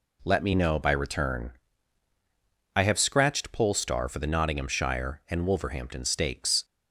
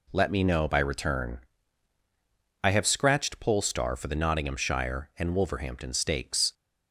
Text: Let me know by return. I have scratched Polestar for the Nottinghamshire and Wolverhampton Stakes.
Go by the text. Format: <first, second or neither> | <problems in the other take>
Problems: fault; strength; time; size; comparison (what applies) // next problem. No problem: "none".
neither | none